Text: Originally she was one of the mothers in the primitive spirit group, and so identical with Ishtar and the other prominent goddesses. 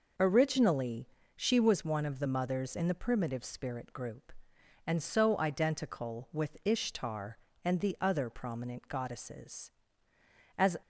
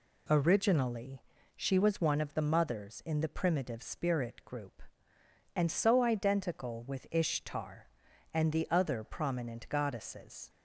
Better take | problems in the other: second | pauses between "Originally" and "she"; slight; at 1.0 s; 0.26 s long; slight in the second // goes on to say "As"; slight; from 10.5 s on; 0.20 s long

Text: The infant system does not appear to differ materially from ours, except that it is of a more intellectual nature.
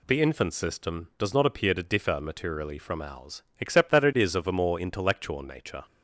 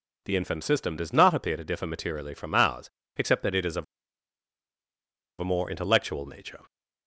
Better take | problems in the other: first | pauses between "of" and "a"; strong; at 3.8 s; 1.5 s long

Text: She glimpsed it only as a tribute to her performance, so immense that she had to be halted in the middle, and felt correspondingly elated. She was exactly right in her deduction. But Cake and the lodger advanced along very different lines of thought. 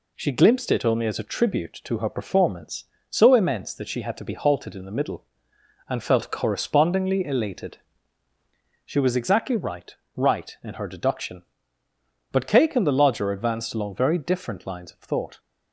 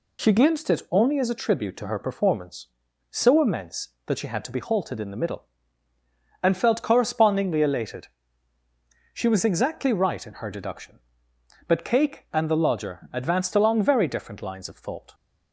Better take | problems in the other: second | says "right" twice; at 10.1 s

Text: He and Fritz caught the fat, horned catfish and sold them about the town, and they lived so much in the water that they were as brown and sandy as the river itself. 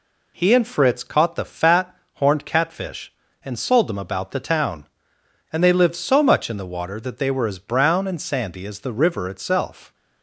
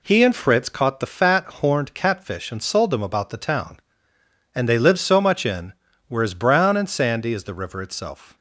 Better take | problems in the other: first | skips "the water that they"; at 5.9 s

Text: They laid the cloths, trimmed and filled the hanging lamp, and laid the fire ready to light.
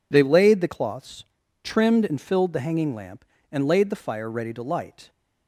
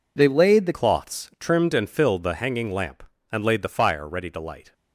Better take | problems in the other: first | changes voice at "cloths"; from 0.7 s on; 4.0 s long

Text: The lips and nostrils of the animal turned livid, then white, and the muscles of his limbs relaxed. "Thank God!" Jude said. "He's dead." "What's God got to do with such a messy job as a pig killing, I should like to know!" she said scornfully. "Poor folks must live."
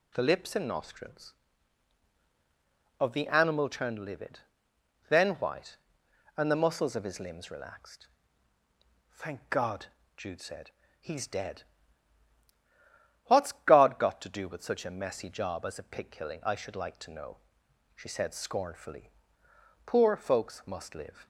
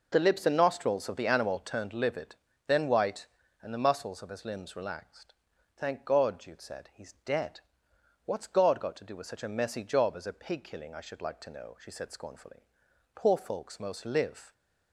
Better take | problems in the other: first | says "most" for "must"; at 13.7 s

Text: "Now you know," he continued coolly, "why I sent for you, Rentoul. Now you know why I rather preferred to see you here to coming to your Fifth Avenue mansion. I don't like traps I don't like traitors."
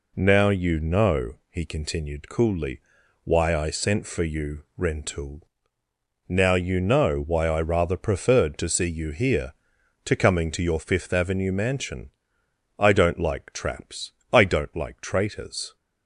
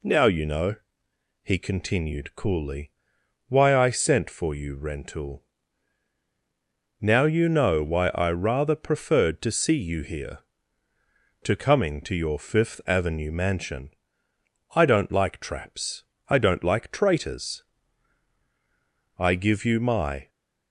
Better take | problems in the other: first | pauses between "traps" and "I"; slight; at 16.0 s; 0.26 s long; slight in the first // goes on to say "I give you my"; noticeable; from 19.1 s on; 1.1 s long

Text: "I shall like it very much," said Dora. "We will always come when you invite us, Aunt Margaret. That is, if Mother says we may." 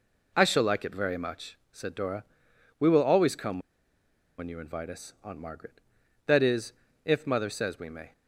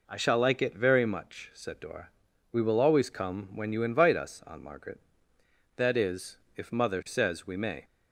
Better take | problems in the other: second | pauses between "come" and "when"; noticeable; at 3.5 s; 0.79 s long

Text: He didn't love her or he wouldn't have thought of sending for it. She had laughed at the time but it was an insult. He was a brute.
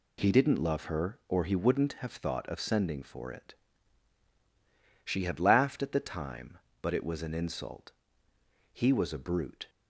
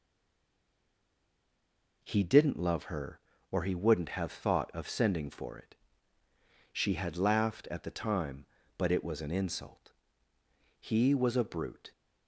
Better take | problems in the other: first | stays silent before the first word; noticeable; until 2.0 s; 2.0 s long

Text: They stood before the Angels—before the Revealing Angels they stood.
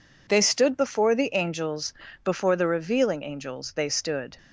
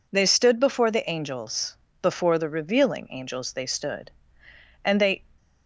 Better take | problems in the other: first | goes on to say "And they"; slight; from 4.8 s on; 0.42 s long

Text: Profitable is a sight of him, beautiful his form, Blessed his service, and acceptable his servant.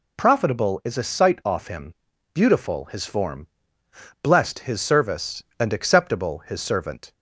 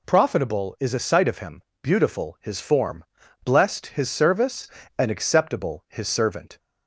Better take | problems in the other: second | says "off" for "of"; at 1.4 s

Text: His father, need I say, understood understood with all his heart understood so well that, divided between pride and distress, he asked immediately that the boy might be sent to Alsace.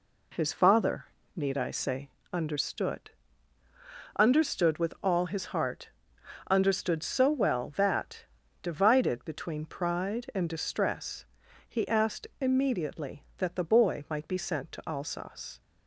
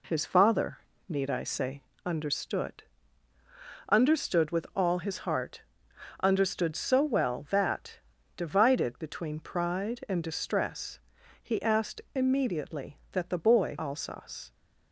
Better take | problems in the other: first | pauses between "understood" and "understood"; at 2.8 s; 1.0 s long; also in the first // pauses between "heart" and "understood"; noticeable; at 5.6 s; 0.62 s long; noticeable in the first // skips "might be sent to"; at 13.7 s

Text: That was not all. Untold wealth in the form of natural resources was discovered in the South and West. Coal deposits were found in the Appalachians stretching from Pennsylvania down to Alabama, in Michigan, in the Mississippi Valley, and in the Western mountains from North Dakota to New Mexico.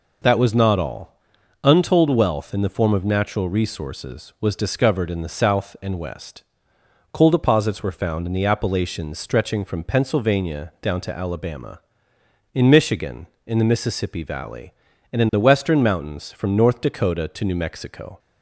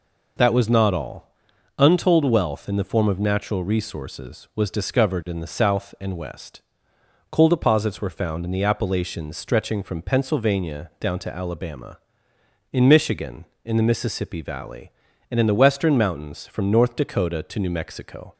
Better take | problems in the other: neither | none

